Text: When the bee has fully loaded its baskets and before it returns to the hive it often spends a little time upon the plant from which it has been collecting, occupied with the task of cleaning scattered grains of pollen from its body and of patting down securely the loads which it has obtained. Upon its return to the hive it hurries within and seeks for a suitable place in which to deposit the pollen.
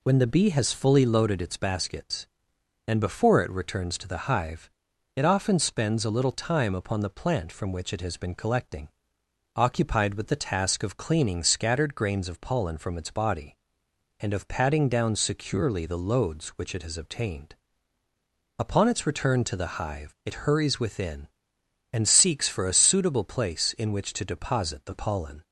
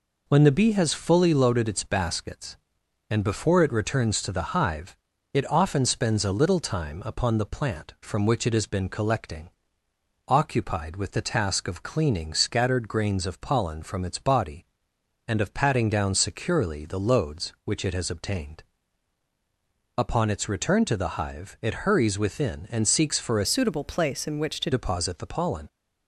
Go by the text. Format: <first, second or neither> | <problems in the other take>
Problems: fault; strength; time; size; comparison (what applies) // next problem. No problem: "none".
first | pauses between "hive" and "it"; at 4.9 s; 0.38 s long; noticeable in the first // changes voice from "suitable" to "to"; from 23.4 to 24.6 s; 1.2 s long